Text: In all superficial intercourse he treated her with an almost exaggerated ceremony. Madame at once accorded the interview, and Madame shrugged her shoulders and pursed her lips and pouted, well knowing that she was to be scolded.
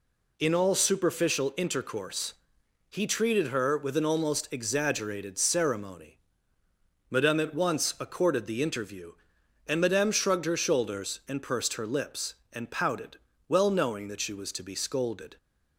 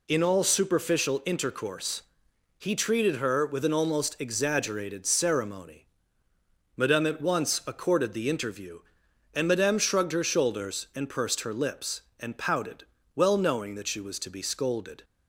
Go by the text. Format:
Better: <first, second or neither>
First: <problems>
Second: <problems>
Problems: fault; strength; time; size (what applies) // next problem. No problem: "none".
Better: neither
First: pauses between "intercourse" and "he"; noticeable; at 2.3 s; 0.56 s long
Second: pauses between "intercourse" and "he"; noticeable; at 2.0 s; 0.56 s long